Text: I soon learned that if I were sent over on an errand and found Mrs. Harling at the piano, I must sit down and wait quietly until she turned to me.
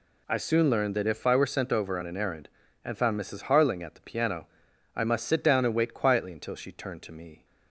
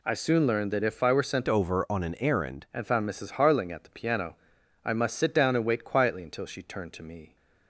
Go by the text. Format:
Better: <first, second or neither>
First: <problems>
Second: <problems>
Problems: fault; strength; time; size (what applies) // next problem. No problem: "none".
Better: first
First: none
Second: changes voice from "over" to "errand"; from 1.4 to 2.6 s; 1.2 s long